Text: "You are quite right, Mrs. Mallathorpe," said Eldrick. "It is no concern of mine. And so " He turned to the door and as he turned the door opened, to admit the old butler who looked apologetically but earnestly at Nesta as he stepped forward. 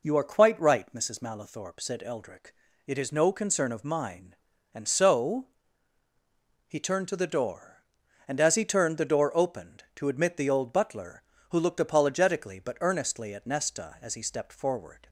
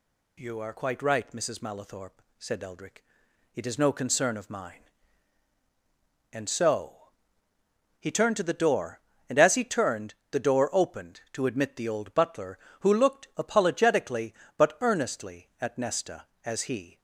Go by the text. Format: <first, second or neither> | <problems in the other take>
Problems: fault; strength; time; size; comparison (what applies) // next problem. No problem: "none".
first | pauses between "turned" and "the"; slight; at 10.1 s; 0.20 s long // stops before "stepped forward"; at 16.9 s